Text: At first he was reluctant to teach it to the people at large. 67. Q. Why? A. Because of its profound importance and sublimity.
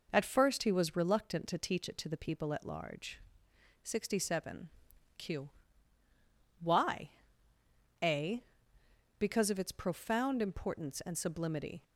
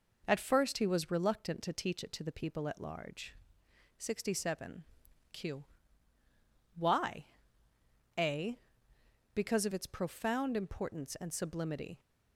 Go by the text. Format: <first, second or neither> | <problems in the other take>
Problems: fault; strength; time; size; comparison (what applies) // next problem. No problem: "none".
neither | none